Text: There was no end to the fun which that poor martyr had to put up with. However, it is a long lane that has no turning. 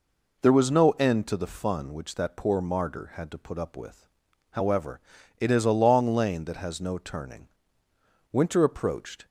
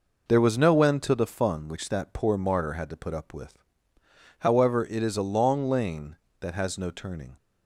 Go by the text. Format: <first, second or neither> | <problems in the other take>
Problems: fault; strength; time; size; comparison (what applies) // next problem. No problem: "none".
second | goes on to say "Winter approached"; noticeable; from 8.3 s on; 0.94 s long